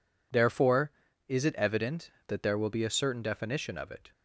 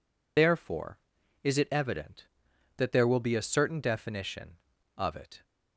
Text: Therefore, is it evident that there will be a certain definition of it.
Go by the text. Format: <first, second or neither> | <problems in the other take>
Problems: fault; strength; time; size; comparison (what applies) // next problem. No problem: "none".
first | loses the start of "Therefore"; at 0.3 s; 45 ms